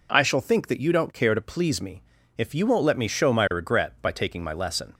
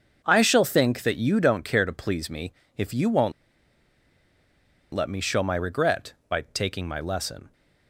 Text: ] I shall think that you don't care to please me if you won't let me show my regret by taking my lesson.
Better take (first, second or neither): first